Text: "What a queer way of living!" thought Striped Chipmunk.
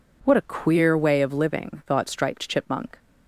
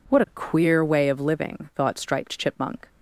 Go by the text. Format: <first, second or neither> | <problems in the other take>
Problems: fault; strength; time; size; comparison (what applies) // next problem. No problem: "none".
neither | none